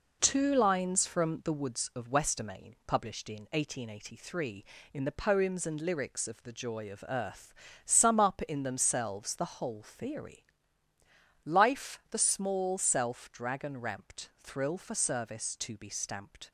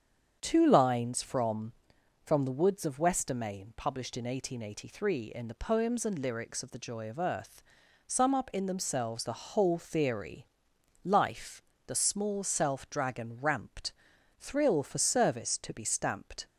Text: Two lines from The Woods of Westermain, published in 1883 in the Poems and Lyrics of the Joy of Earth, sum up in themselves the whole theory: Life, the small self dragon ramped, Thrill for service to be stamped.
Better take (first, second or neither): first